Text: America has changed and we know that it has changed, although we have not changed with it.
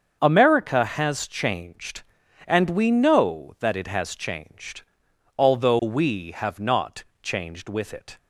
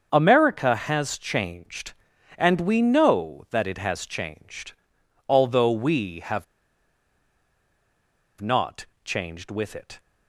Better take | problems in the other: first | starts louder than the rest; until 1.1 s; 7 dB; also in the first // pauses between "have" and "not"; strong; at 6.4 s; 1.9 s long // pauses between "not" and "changed"; slight; at 8.8 s; 0.20 s long; slight in the first

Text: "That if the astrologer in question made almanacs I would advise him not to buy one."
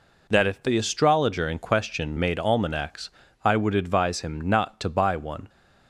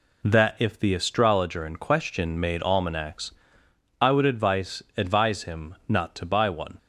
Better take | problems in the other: first | pauses between "almanacs" and "I"; noticeable; at 3.3 s; 0.68 s long; slight in the first // says "advise" twice; at 4.9 s

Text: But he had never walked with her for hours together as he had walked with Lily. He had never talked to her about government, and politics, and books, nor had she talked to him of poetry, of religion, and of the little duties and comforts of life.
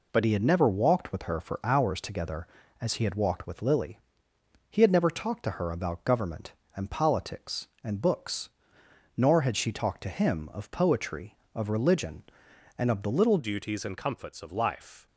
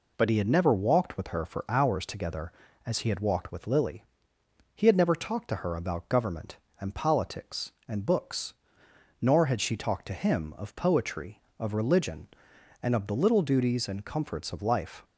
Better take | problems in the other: second | changes voice at "duties"; from 13.3 s on; 1.7 s long

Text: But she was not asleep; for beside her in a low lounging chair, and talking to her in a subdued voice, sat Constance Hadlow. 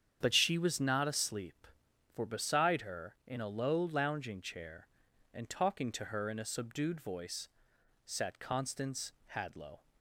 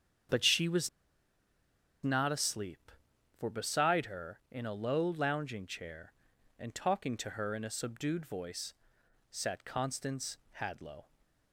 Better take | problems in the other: first | starts louder than the rest; strong; until 2.4 s; 8 dB; strong in the first // pauses between "was" and "not"; at 0.8 s; 1.1 s long // pauses between "Constance" and "Hadlow"; slight; at 10.3 s; 0.20 s long; slight in the first

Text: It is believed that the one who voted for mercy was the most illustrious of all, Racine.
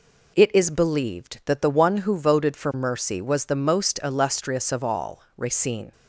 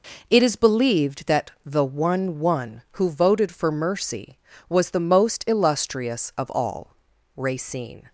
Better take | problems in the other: first | says "one" twice; at 2.3 s

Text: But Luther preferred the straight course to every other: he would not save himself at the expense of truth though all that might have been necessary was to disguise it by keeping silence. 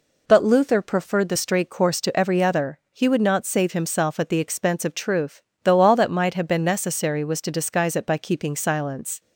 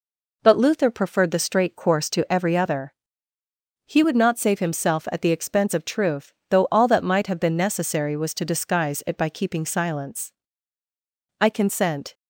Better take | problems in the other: first | pauses between "truth" and "though"; slight; at 6.3 s; 0.18 s long; slight in the first // goes on to say "I consent"; noticeable; from 11.4 s on; 0.72 s long

